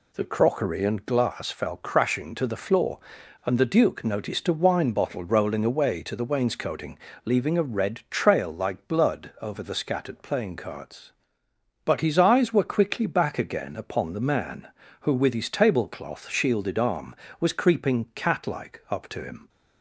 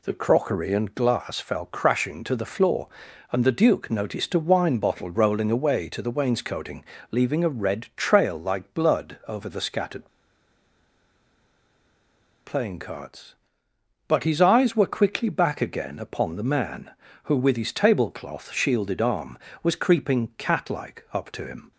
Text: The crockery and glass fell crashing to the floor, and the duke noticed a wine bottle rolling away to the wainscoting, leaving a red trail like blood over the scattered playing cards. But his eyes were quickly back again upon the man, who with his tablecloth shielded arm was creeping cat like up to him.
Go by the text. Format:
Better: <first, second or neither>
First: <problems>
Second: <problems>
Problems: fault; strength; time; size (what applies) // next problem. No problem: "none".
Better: first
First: none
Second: pauses between "scattered" and "playing"; strong; at 10.0 s; 2.3 s long